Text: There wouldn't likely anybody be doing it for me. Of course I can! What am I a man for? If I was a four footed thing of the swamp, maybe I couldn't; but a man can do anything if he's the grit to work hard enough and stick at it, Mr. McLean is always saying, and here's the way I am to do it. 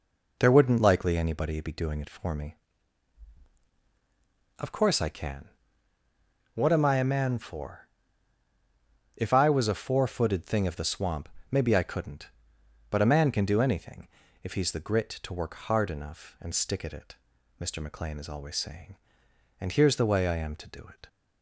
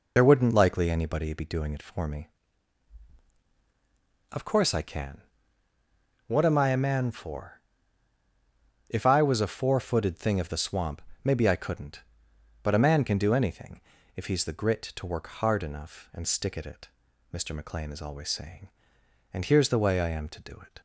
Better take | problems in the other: first | loses the start of "There"; at 0.1 s; 35 ms // pauses between "anything" and "if"; slight; at 13.8 s; 0.36 s long; slight in the first

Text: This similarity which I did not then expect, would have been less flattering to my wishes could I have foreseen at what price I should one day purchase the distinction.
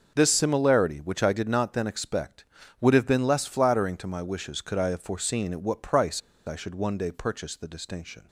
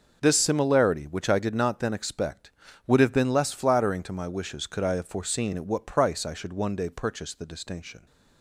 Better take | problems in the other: second | pauses between "price" and "I"; slight; at 6.2 s; 0.26 s long

